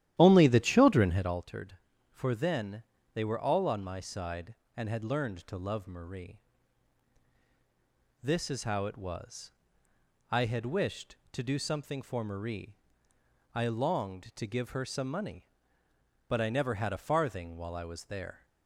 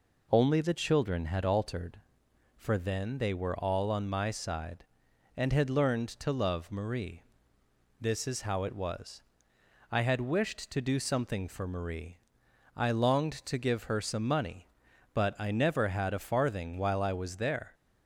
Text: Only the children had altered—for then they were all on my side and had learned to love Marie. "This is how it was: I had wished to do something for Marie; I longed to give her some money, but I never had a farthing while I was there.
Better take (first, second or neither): second